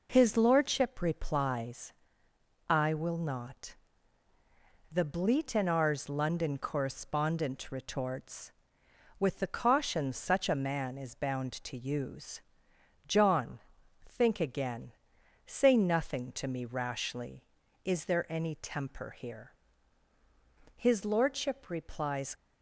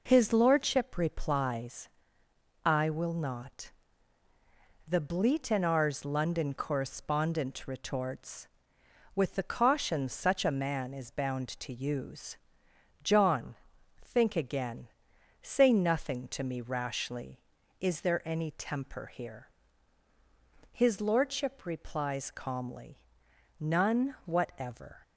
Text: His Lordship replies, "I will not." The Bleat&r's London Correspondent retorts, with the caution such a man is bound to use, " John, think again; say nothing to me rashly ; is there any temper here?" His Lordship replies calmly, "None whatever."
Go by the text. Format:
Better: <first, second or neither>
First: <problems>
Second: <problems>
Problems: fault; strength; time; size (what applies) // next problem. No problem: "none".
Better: second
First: stops before "calmly None whatever"; at 22.3 s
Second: none